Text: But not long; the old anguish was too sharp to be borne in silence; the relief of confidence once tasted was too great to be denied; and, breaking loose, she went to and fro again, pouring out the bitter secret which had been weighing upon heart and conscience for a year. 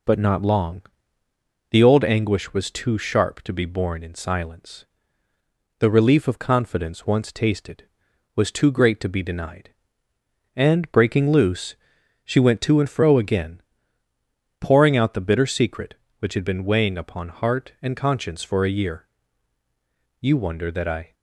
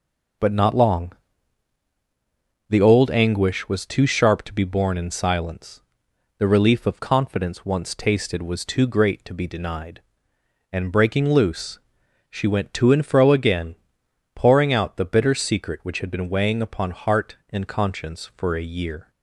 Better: second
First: goes on to say "You wonder that I"; noticeable; from 20.1 s on; 0.94 s long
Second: none

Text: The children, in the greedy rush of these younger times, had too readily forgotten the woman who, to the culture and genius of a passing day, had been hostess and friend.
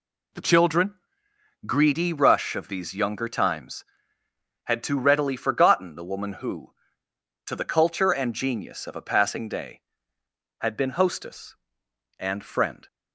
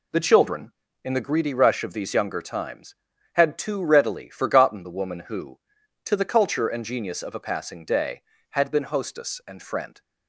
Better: second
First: skips "in the"; at 1.3 s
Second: none

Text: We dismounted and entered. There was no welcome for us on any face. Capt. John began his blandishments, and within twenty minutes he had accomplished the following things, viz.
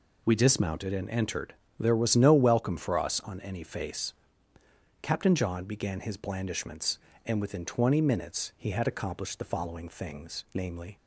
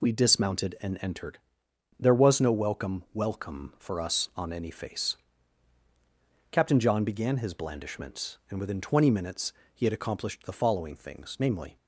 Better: first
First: none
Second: says "welcome" twice; at 3.1 s // pauses between "minutes" and "he"; slight; at 9.5 s; 0.24 s long

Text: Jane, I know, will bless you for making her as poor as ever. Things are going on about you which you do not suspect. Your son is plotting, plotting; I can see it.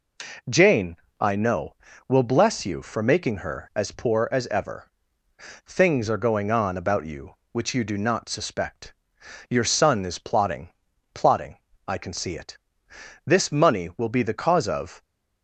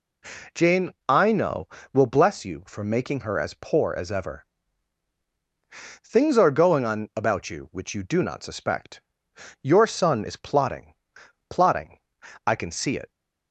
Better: second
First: goes on to say "This money will be the cause of"; strong; from 13.2 s on; 1.7 s long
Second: none

